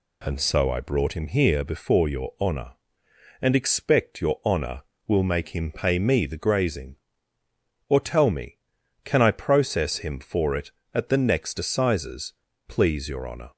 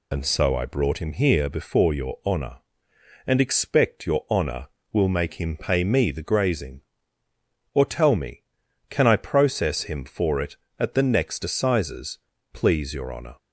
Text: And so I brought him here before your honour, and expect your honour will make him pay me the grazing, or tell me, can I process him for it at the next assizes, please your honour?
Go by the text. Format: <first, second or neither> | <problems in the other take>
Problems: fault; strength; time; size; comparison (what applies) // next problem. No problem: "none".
first | loses the start of "And"; at 0.1 s; 50 ms